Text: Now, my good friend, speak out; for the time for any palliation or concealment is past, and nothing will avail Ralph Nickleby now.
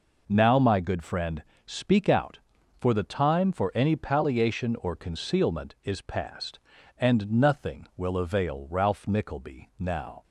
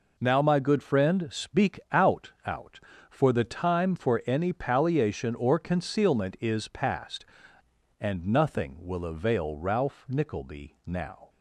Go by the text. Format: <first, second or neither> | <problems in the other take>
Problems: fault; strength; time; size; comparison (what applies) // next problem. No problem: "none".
first | says "out" twice; at 2.4 s